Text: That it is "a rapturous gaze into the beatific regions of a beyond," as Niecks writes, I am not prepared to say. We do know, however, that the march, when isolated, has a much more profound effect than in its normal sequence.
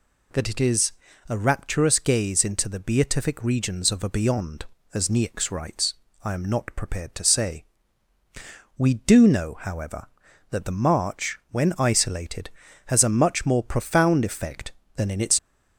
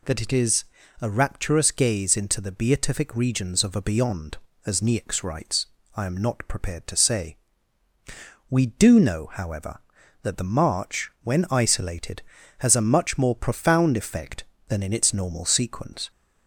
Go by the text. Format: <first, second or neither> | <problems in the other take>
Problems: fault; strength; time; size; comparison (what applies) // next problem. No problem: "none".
second | pauses between "is" and "a"; slight; at 0.9 s; 0.36 s long; slight in the second // stops before "normal sequence"; at 15.3 s